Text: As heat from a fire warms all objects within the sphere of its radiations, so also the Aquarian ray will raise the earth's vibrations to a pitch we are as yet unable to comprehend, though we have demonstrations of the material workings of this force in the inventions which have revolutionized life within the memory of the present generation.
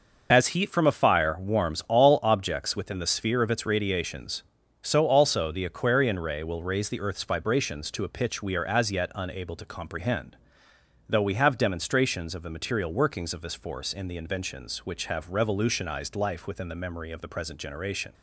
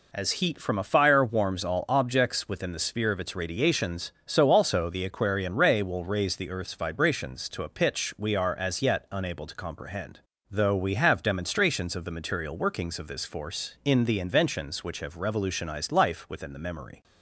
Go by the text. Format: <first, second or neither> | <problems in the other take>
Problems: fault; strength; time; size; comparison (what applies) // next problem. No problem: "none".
first | stops before "of the present generation"; at 17.0 s